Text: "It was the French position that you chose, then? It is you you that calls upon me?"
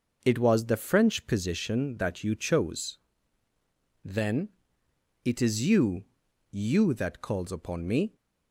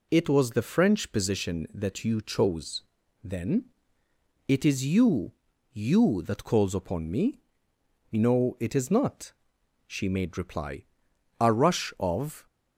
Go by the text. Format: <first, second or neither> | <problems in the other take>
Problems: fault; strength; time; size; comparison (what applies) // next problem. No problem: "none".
first | pauses between "you" and "you"; at 5.3 s; 0.44 s long; also in the first // goes on to say "No it is not she made reply a rush of"; strong; from 8.1 s on; 4.3 s long